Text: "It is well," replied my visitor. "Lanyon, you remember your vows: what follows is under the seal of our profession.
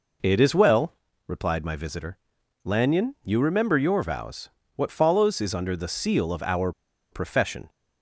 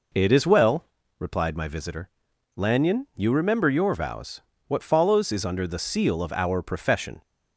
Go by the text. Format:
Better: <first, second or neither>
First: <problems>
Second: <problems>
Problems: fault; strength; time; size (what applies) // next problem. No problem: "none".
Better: second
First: pauses between "our" and "profession"; at 6.7 s; 0.40 s long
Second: none